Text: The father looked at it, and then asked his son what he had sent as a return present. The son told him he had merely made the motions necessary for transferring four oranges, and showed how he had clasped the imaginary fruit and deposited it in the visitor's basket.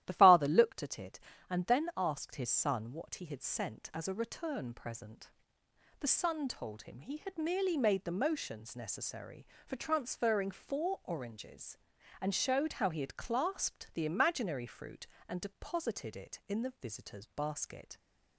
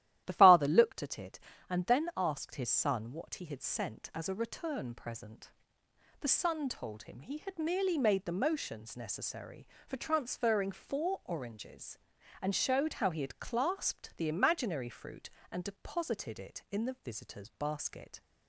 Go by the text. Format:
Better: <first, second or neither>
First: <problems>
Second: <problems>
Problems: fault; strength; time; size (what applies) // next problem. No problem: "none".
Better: neither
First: starts louder than the rest; strong; until 1.0 s; 13 dB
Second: starts louder than the rest; strong; until 1.2 s; 13 dB